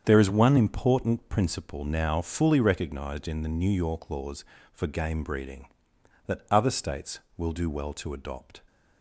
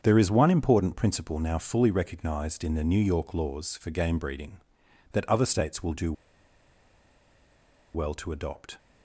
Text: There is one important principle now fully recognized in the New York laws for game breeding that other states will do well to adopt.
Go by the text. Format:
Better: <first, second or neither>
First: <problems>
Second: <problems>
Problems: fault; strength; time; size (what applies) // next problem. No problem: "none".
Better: first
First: starts louder than the rest; strong; until 1.0 s; 7.5 dB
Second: starts louder than the rest; strong; until 1.0 s; 7 dB // pauses between "do" and "well"; strong; at 6.1 s; 1.8 s long